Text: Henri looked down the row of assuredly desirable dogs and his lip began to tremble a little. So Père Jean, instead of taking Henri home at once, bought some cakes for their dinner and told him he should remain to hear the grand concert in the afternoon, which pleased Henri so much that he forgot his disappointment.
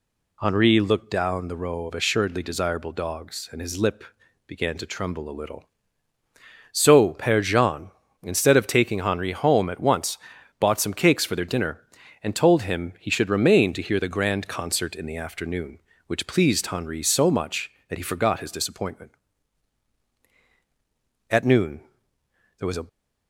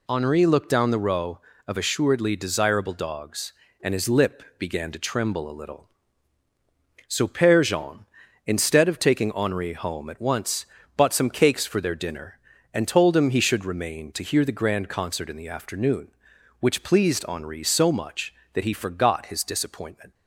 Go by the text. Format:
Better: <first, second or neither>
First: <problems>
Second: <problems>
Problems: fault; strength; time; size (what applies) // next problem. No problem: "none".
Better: second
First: pauses between "lip" and "began"; at 4.0 s; 0.44 s long // goes on to say "At noon there was a"; from 21.2 s on; 1.5 s long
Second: none